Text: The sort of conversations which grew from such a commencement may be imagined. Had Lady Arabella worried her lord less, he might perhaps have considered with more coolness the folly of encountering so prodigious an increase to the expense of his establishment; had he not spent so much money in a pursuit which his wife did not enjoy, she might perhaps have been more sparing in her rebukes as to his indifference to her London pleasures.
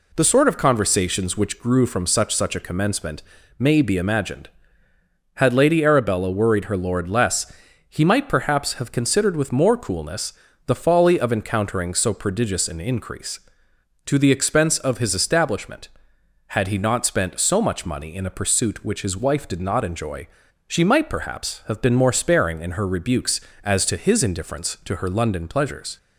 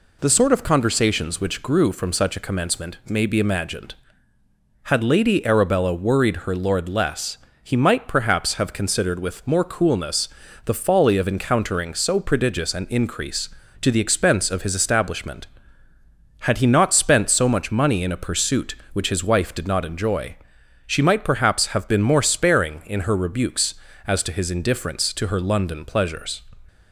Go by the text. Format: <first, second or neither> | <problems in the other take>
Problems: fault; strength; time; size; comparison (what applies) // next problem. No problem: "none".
second | says "such" twice; at 2.3 s // pauses between "commencement" and "may"; slight; at 3.2 s; 0.34 s long // pauses between "coolness" and "the"; slight; at 10.3 s; 0.34 s long; also in the second